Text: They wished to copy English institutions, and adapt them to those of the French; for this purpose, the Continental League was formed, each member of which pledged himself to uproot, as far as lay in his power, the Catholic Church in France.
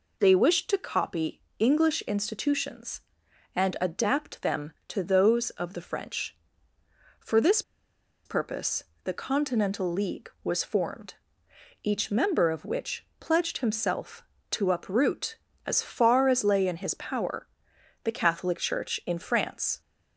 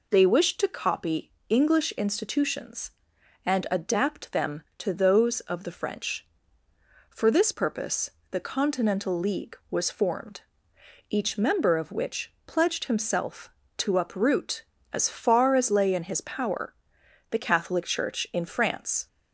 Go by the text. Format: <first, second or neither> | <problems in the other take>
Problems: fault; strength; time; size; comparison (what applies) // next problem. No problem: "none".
second | pauses between "copy" and "English"; slight; at 1.4 s; 0.18 s long; slight in the second // pauses between "this" and "purpose"; noticeable; at 7.6 s; 0.64 s long